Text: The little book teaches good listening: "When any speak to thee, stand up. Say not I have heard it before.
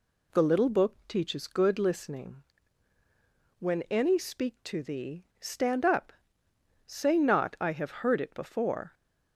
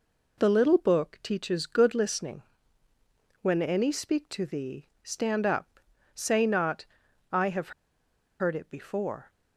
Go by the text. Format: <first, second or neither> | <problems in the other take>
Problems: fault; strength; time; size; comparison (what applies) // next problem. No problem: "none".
first | pauses between "not" and "I"; noticeable; at 6.8 s; 0.48 s long // pauses between "have" and "heard"; noticeable; at 7.7 s; 0.68 s long